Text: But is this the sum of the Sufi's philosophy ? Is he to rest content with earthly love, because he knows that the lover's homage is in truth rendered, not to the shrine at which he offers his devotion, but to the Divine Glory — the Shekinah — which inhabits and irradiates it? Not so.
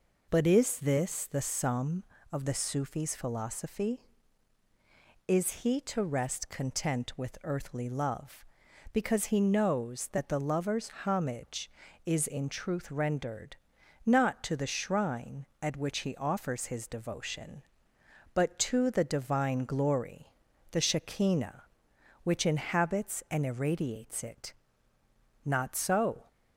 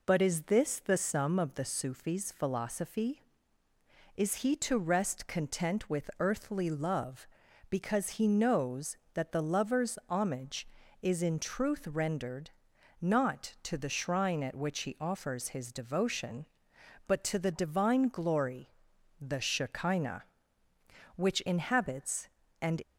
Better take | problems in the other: first | stops before "irradiates it Not so"; at 22.8 s

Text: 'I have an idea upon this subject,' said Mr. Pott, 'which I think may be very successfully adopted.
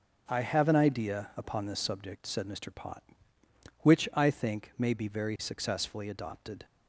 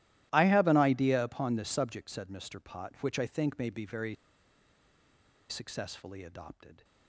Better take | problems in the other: first | starts louder than the rest; strong; until 1.3 s; 14.5 dB; noticeable in the first // pauses between "very" and "successfully"; strong; at 4.1 s; 1.3 s long

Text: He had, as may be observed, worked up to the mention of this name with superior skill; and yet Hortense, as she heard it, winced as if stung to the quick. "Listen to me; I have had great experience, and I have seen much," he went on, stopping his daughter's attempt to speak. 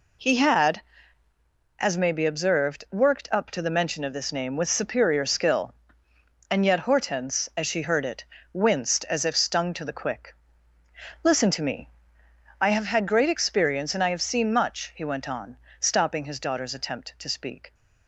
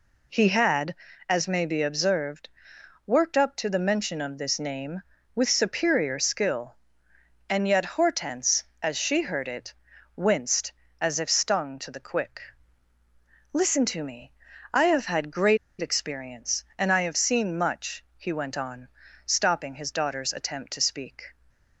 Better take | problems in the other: first | pauses between "great" and "experience"; slight; at 15.5 s; 0.24 s long

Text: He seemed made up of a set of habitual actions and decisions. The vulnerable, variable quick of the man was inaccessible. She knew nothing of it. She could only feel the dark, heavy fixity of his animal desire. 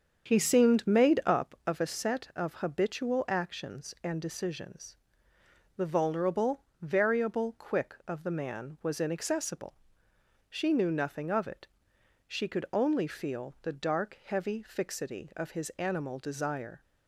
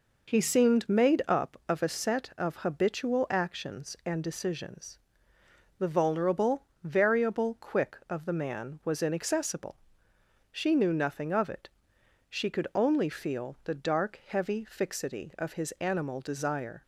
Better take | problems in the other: second | starts louder than the rest; strong; until 1.6 s; 7 dB

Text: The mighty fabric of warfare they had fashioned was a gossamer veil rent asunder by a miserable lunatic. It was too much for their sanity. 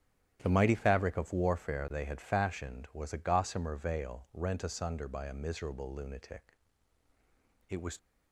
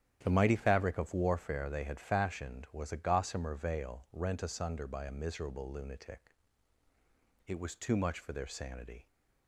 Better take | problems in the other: second | starts louder than the rest; strong; until 1.4 s; 11 dB; strong in the second // stops before "too much for their sanity"; at 7.9 s

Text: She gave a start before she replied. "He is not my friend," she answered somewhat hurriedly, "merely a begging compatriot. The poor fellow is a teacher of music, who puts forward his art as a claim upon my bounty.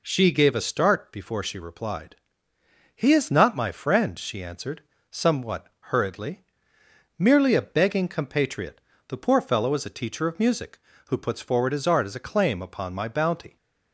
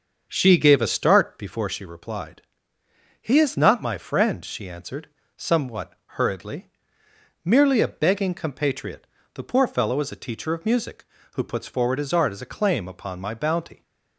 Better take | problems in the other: first | starts louder than the rest; until 1.7 s; 6.5 dB // pauses between "answered" and "somewhat"; slight; at 5.0 s; 0.28 s long; slight in the first // pauses between "somewhat" and "hurriedly"; slight; at 5.9 s; 0.24 s long; slight in the first

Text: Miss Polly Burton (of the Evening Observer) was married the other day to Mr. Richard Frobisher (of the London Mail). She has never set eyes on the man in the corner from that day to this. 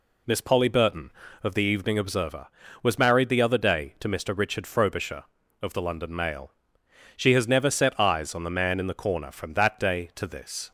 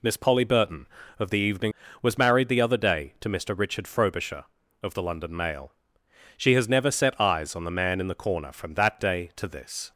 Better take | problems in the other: first | skips "Observer"; at 1.8 s

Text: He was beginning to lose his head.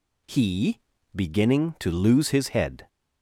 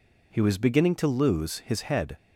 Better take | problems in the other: second | skips "was"; at 0.9 s

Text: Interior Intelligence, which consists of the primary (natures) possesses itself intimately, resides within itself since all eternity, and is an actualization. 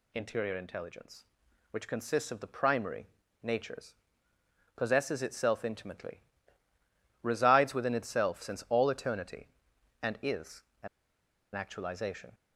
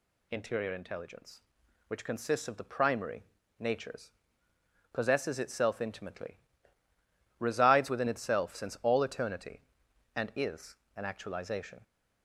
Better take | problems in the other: second | pauses between "is" and "an"; slight; at 10.6 s; 0.20 s long; slight in the second // pauses between "an" and "actualization"; noticeable; at 10.8 s; 0.67 s long

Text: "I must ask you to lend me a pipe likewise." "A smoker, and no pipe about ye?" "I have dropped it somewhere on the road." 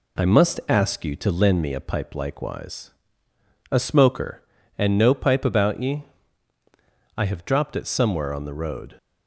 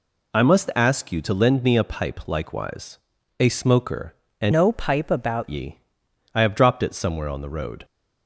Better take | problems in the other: first | changes voice from "no" to "about"; from 4.5 to 5.4 s; 0.9 s long

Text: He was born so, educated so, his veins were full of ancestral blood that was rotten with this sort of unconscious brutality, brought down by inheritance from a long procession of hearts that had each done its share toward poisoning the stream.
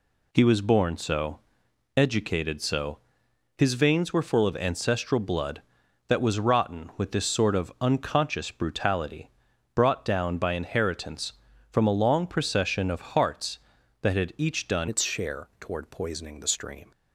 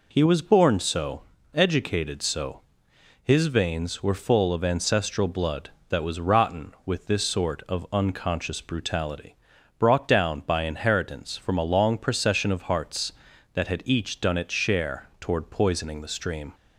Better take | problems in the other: second | changes voice at "its"; from 14.8 s on; 2.1 s long

